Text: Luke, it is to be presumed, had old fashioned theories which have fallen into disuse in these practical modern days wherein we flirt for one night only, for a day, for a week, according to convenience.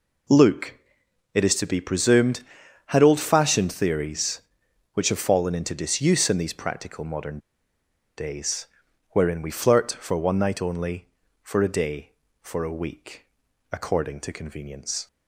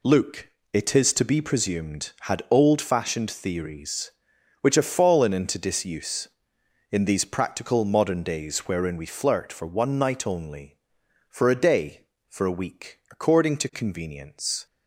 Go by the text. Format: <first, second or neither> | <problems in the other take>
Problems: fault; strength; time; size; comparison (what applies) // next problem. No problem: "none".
second | pauses between "modern" and "days"; noticeable; at 7.3 s; 0.78 s long // pauses between "days" and "wherein"; at 8.6 s; 0.42 s long